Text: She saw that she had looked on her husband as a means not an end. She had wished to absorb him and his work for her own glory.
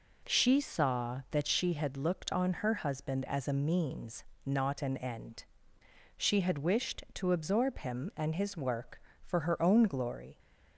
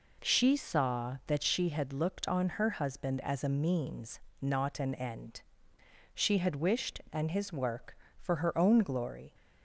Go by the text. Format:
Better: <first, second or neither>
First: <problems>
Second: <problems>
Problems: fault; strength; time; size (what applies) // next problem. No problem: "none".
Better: first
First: pauses between "means" and "not"; slight; at 4.2 s; 0.22 s long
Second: pauses between "means" and "not"; slight; at 4.1 s; 0.22 s long // skips "to absorb him"; at 7.0 s